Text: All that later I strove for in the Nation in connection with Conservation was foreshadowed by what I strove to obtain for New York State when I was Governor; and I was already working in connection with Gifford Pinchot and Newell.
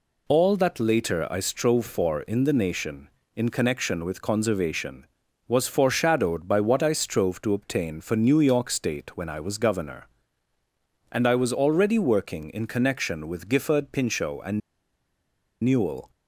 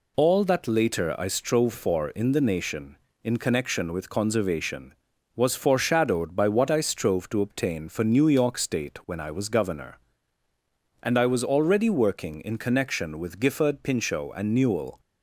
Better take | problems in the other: second | pauses between "and" and "Newell"; at 14.6 s; 1.0 s long

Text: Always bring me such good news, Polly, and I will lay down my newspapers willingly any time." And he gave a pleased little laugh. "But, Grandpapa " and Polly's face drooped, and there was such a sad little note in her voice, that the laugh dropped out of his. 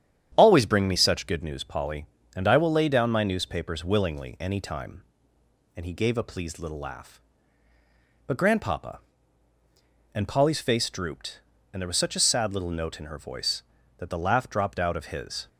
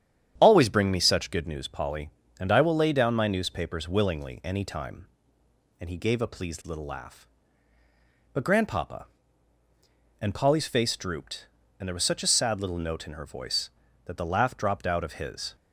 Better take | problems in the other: neither | starts louder than the rest; strong; the same in both

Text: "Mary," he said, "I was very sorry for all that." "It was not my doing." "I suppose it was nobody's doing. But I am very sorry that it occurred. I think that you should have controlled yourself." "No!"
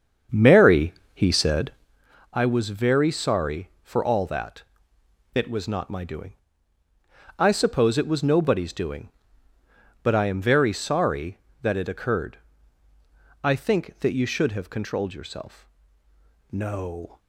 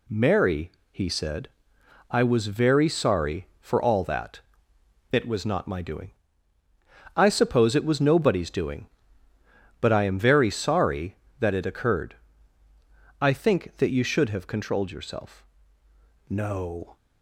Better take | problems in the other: second | starts louder than the rest; strong; until 2.0 s; 7 dB

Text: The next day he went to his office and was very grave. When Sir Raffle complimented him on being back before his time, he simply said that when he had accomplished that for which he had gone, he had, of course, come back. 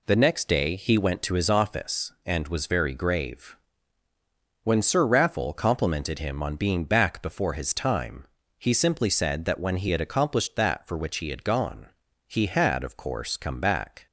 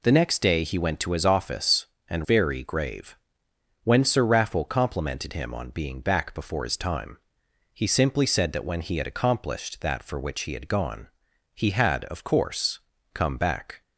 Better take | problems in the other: first | skips "was"; at 2.2 s

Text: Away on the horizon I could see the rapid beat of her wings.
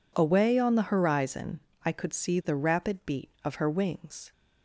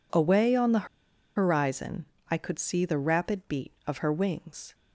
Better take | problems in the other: first | pauses between "the" and "horizon"; noticeable; at 0.8 s; 0.48 s long // pauses between "horizon" and "I"; slight; at 2.0 s; 0.28 s long; slight in the first

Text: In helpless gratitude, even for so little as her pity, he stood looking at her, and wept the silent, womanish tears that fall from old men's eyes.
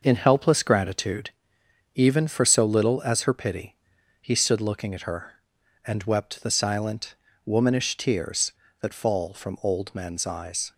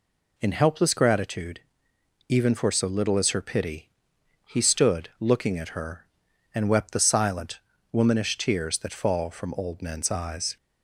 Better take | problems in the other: second | gets quieter; noticeable; throughout; 6 dB

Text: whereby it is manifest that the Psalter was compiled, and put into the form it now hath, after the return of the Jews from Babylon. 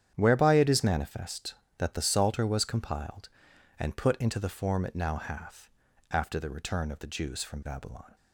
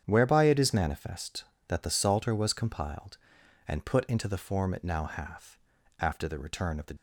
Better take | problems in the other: first | starts louder than the rest; strong; until 1.0 s; 8.5 dB; strong in the first // stops before "Jews from Babylon"; at 6.9 s

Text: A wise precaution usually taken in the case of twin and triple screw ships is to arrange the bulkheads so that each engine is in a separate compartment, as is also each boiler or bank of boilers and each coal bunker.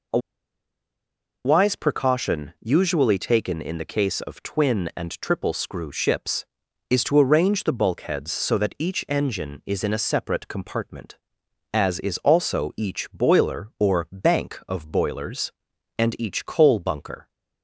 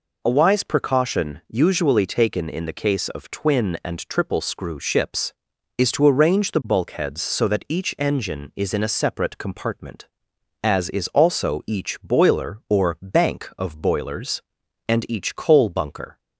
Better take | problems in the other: second | pauses between "A" and "wise"; strong; at 0.1 s; 1.2 s long

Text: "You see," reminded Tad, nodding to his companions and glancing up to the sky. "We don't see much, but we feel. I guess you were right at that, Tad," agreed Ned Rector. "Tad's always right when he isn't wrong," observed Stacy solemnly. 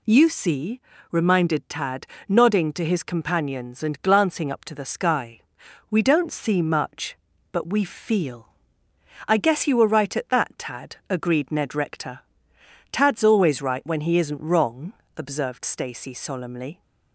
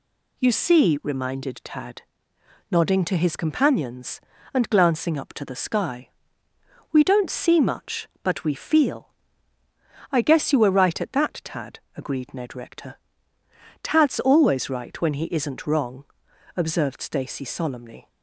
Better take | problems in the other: neither | none

